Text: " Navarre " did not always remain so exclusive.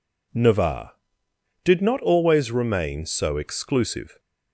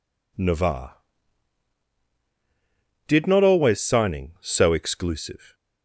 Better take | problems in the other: first | says "signing" for "remain"; at 3.7 s

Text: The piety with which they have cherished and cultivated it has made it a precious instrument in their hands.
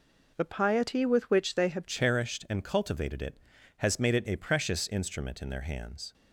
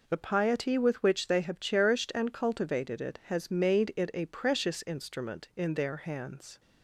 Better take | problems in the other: second | changes voice at "cherished"; from 1.8 s on; 4.3 s long

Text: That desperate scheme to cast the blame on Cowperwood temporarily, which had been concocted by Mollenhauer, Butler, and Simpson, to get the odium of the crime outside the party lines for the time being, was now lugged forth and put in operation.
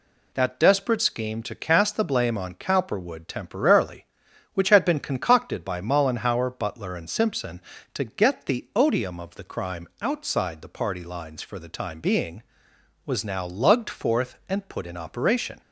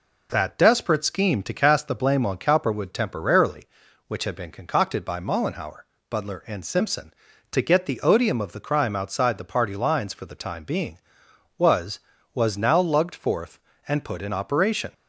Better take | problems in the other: first | says "was" twice; at 12.3 s

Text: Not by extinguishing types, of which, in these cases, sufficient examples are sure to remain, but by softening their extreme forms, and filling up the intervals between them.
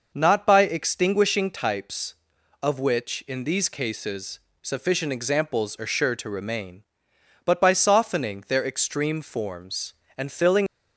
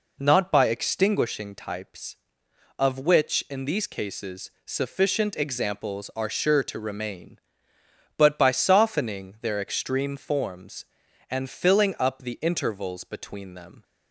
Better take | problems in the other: second | stops before "up the intervals between them"; at 10.6 s

